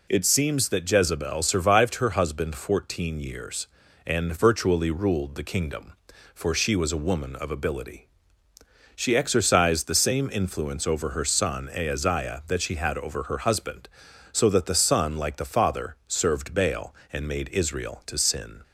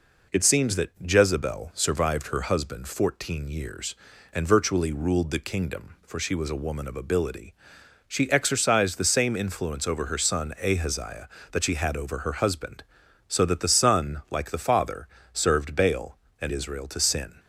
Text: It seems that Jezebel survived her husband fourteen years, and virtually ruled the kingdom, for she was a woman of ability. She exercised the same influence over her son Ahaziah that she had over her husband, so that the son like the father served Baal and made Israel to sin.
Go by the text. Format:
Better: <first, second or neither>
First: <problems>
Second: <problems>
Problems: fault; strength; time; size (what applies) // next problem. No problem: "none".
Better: first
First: none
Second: pauses between "father" and "served"; slight; at 15.0 s; 0.26 s long // skips "made"; at 16.5 s